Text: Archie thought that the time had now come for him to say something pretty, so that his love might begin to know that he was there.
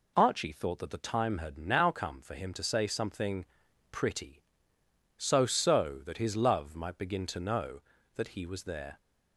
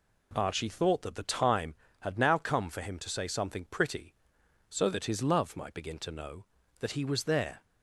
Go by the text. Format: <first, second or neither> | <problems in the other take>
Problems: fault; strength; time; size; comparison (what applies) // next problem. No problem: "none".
second | pauses between "something" and "pretty"; noticeable; at 3.4 s; 0.46 s long // says "so" twice; at 5.4 s